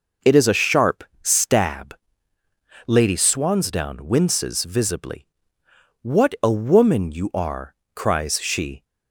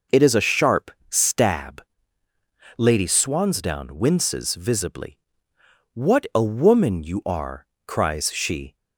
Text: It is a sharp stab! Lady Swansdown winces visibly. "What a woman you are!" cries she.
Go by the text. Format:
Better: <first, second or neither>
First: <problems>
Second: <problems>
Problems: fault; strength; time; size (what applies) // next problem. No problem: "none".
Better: neither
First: pauses between "sharp" and "stab"; slight; at 1.0 s; 0.20 s long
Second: pauses between "sharp" and "stab"; slight; at 0.9 s; 0.20 s long